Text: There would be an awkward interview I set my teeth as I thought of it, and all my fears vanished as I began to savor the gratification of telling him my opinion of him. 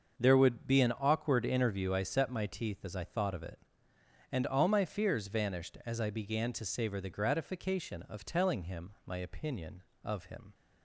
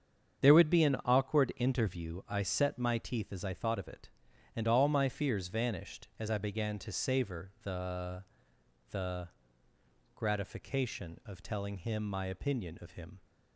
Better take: first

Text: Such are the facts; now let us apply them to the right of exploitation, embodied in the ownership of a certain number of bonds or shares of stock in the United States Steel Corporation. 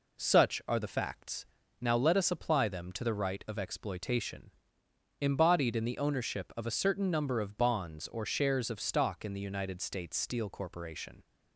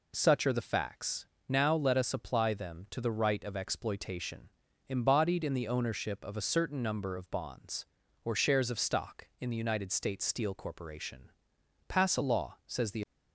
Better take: first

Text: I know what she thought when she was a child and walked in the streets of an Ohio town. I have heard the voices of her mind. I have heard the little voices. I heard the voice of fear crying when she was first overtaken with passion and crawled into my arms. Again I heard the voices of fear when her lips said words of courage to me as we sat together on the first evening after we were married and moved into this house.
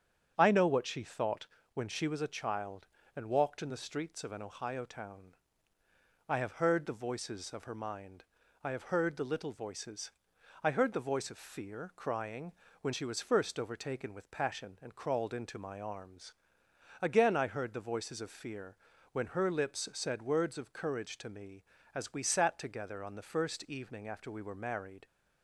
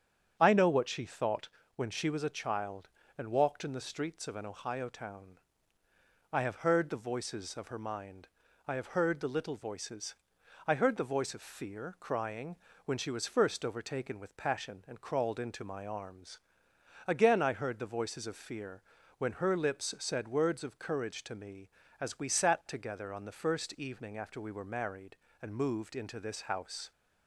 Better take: second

